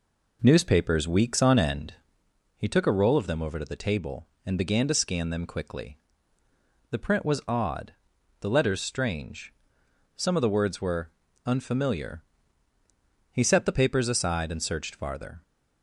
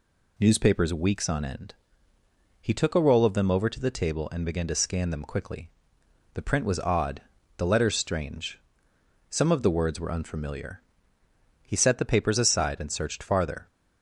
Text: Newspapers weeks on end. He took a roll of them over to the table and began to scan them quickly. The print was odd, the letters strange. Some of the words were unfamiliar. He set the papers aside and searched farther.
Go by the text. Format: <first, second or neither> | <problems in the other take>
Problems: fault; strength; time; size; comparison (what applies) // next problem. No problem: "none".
second | starts louder than the rest; noticeable; until 2.1 s; 4 dB // pauses between "were" and "unfamiliar"; slight; at 11.1 s; 0.34 s long